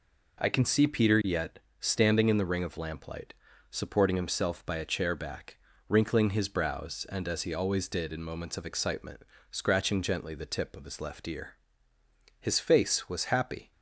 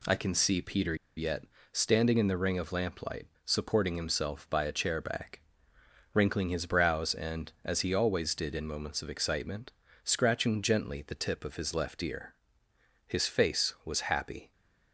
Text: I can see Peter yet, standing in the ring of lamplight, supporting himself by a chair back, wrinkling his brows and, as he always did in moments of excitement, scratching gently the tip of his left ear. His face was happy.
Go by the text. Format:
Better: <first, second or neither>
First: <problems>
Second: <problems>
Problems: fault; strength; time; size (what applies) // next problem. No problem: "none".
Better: first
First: none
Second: pauses between "Peter" and "yet"; slight; at 0.9 s; 0.20 s long